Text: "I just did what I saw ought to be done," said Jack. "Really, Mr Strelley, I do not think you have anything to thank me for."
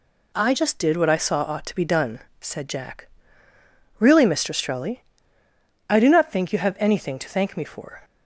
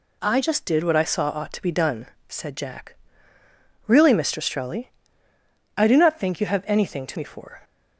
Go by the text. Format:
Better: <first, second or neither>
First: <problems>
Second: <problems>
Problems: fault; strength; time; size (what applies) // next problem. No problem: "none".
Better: first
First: none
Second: skips "thank"; at 7.1 s